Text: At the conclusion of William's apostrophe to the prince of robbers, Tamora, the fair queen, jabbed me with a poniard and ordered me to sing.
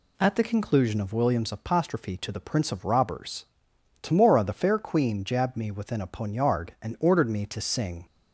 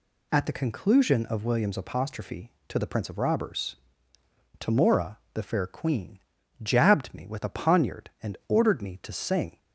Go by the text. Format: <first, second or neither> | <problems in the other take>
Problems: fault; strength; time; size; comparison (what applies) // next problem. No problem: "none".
second | says "within" for "with"; at 5.7 s